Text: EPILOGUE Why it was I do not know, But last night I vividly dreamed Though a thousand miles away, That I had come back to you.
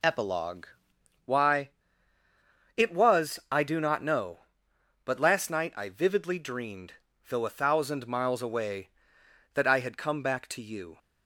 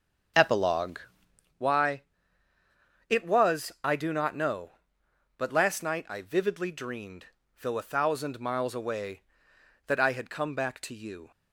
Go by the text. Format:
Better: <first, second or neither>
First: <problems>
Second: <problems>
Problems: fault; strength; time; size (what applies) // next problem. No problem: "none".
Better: first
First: pauses between "EPILOGUE" and "Why"; noticeable; at 0.6 s; 0.58 s long // pauses between "Why" and "it"; at 1.7 s; 1.0 s long // pauses between "dreamed" and "Though"; at 6.9 s; 0.38 s long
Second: starts louder than the rest; until 1.6 s; 7 dB // pauses between "EPILOGUE" and "Why"; noticeable; at 1.0 s; 0.58 s long // pauses between "Why" and "it"; at 2.0 s; 1.0 s long // pauses between "dreamed" and "Though"; at 7.2 s; 0.38 s long